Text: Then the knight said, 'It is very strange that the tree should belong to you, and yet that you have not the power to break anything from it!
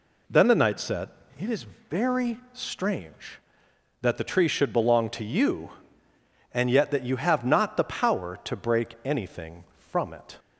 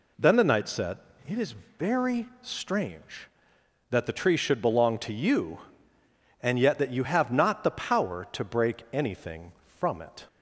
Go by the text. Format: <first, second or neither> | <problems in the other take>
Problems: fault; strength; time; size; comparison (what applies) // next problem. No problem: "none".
neither | pauses between "is" and "very"; slight; the same in both